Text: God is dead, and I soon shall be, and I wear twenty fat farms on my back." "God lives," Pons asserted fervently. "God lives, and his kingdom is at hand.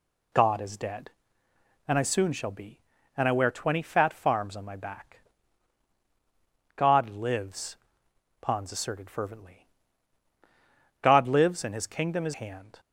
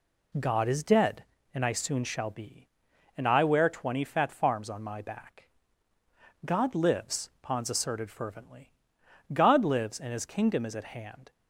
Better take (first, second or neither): second